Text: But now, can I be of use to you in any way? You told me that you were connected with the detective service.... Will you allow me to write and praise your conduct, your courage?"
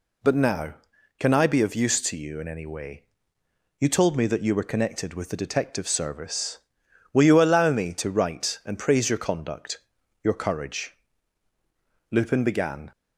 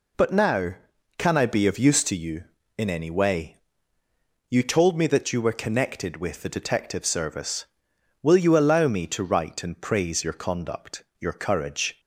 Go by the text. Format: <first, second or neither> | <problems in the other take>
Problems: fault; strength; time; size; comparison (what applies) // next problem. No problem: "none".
second | goes on to say "Lupin began"; noticeable; from 12.0 s on; 0.82 s long